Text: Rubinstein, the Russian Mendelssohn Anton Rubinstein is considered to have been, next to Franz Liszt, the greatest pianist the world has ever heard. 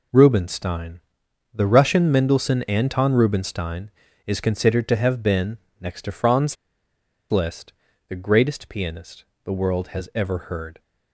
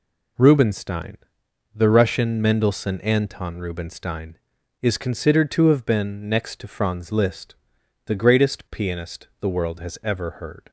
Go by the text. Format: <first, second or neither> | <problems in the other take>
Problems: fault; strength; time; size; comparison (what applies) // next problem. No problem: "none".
second | pauses between "Franz" and "Liszt"; noticeable; at 6.5 s; 0.75 s long // pauses between "pianist" and "the"; slight; at 9.2 s; 0.20 s long